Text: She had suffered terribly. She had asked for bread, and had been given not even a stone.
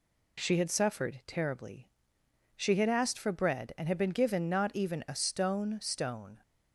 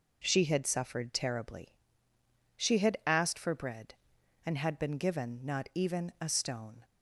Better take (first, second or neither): second